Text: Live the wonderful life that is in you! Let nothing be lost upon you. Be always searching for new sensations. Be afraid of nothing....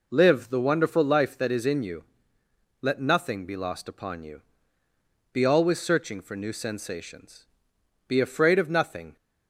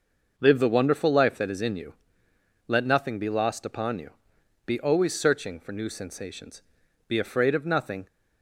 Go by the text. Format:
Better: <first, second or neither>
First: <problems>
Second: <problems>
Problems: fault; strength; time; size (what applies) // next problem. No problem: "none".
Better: neither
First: none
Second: none